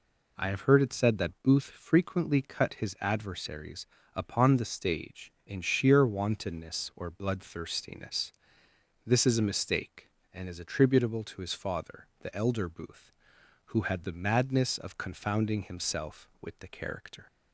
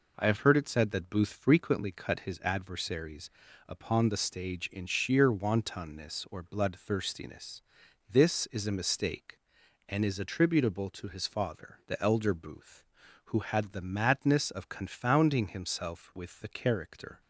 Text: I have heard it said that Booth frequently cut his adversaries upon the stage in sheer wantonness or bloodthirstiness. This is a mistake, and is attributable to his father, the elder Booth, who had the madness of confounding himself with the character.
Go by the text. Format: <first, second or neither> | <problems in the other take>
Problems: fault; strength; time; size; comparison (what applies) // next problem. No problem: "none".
neither | pauses between "adversaries" and "upon"; slight; the same in both